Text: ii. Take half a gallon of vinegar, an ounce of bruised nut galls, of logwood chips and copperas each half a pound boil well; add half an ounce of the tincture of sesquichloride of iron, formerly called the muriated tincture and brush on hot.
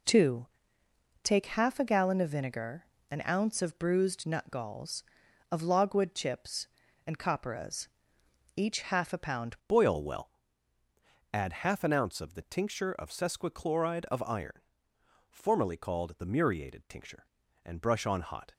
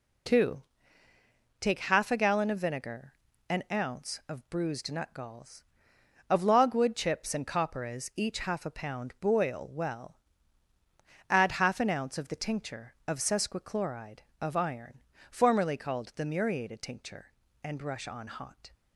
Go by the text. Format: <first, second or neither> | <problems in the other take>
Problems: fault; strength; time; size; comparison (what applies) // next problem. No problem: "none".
second | pauses between "copperas" and "each"; noticeable; at 7.8 s; 0.70 s long // changes voice at "boil"; from 9.6 s on; 8.9 s long